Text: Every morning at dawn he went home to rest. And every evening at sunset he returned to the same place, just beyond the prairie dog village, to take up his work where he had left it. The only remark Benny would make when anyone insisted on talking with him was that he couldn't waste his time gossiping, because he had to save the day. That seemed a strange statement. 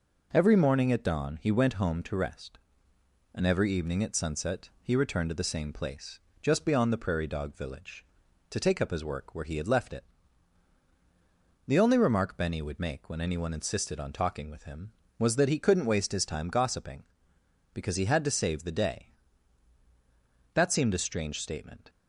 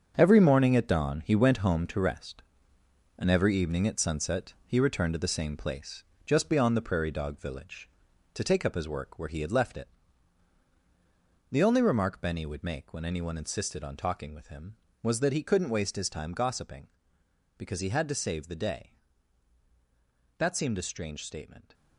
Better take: first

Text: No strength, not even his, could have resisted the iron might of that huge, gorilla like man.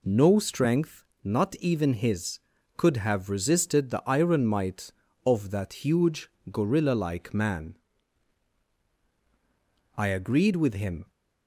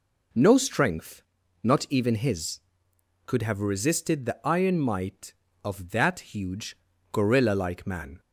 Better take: second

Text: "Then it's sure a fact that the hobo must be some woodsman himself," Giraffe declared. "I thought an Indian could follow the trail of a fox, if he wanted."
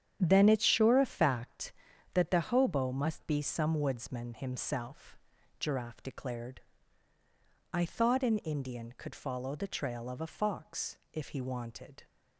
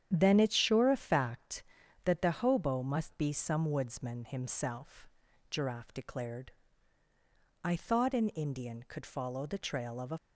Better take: first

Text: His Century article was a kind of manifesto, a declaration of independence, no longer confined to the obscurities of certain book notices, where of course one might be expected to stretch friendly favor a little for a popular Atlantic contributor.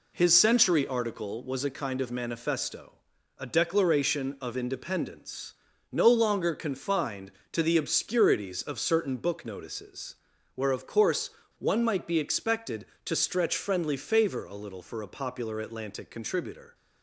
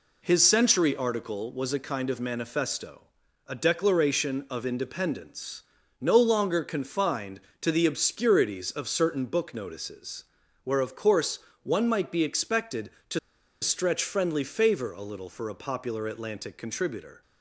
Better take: first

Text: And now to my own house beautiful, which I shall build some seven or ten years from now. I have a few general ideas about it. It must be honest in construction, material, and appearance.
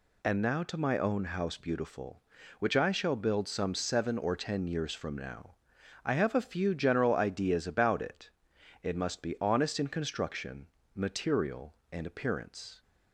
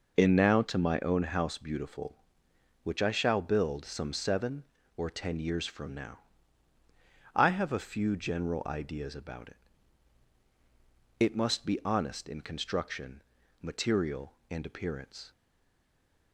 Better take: first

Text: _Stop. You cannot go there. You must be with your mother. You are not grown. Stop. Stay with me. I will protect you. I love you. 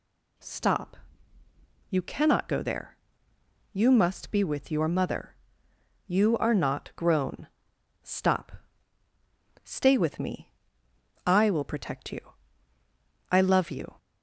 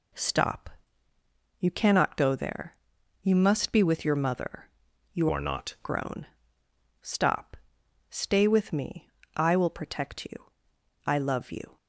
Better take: first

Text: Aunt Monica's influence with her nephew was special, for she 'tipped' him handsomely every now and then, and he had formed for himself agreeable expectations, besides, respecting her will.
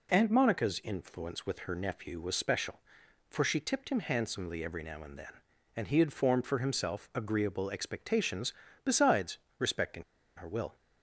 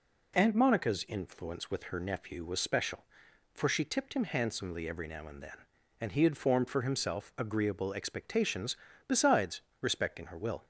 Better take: second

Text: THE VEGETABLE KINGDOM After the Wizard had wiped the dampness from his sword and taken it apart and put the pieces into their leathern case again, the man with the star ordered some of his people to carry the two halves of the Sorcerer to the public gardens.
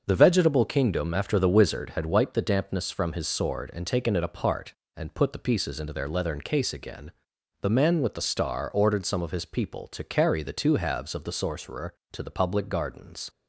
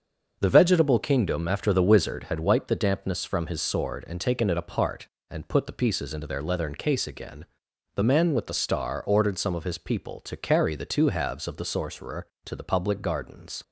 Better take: neither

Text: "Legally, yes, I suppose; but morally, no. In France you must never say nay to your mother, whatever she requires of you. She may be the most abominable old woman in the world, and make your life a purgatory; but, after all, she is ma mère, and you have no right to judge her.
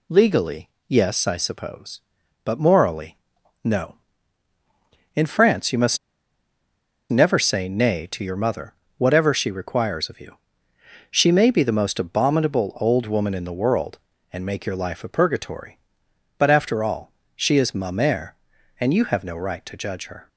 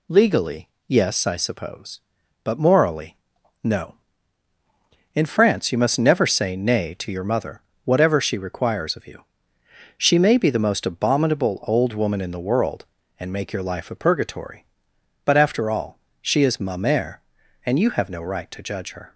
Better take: second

